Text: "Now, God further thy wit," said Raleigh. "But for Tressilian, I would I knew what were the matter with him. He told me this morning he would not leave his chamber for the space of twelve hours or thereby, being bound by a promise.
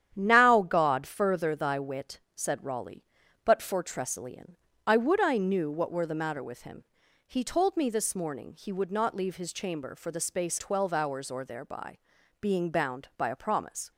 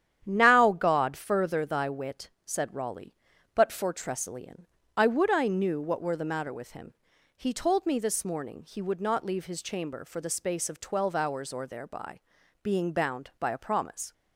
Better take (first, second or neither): second